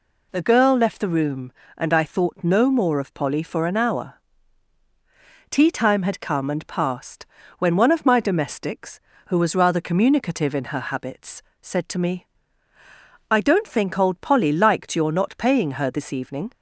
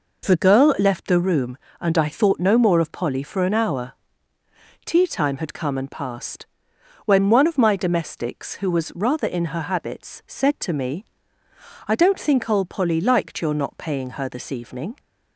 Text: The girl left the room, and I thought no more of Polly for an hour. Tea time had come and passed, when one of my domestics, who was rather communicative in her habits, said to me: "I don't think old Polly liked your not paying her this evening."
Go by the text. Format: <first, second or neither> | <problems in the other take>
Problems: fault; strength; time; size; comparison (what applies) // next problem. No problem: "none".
first | skips "communicative"; at 9.2 s